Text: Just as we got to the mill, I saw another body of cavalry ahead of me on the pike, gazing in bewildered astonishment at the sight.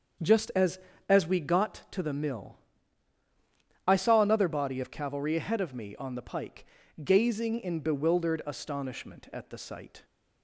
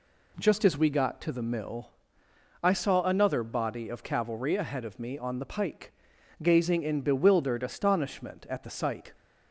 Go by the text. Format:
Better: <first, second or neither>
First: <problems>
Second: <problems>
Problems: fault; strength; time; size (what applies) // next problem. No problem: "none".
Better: second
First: starts louder than the rest; until 1.5 s; 6.5 dB // says "as" twice; at 1.0 s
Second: none